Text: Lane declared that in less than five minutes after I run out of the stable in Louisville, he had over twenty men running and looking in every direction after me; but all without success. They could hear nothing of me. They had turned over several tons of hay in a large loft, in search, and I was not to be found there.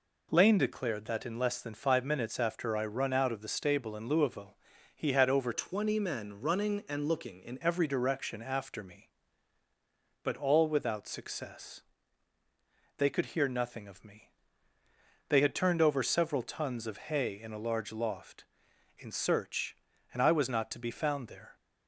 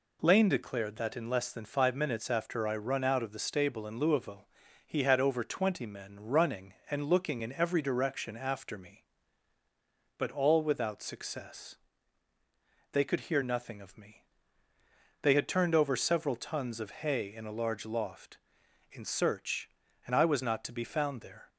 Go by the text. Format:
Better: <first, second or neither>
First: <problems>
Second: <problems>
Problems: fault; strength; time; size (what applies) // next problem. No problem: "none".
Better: second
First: changes voice from "twenty" to "in"; from 5.5 to 7.5 s; 2.0 s long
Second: none